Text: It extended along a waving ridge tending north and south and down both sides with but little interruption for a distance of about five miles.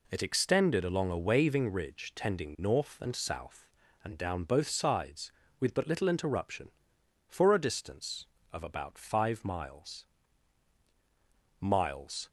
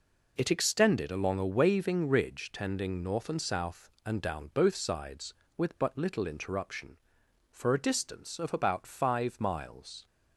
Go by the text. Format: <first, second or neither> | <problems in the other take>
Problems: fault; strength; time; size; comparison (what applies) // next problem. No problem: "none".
second | says "miles" twice; at 11.6 s